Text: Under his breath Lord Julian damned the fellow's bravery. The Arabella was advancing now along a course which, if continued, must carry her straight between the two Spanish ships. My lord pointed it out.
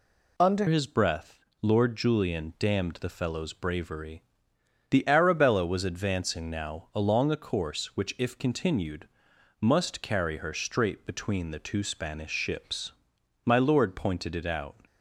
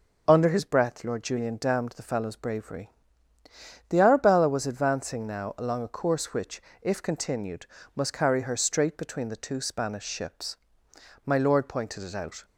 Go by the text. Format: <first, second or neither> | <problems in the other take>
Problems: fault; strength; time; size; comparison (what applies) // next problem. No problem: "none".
second | changes voice at "his"; from 0.6 s on; 14.1 s long // pauses between "breath" and "Lord"; slight; at 1.4 s; 0.22 s long